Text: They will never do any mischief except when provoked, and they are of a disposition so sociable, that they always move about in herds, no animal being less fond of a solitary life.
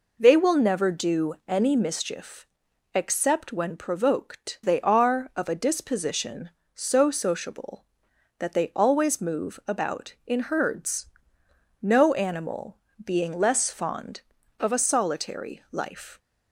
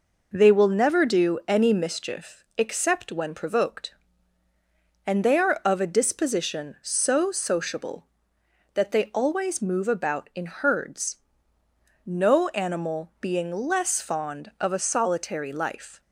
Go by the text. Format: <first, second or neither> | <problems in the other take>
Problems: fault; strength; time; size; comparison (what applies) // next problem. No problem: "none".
second | pauses between "mischief" and "except"; noticeable; at 2.4 s; 0.46 s long // skips "and"; at 4.6 s // pauses between "animal" and "being"; slight; at 12.7 s; 0.28 s long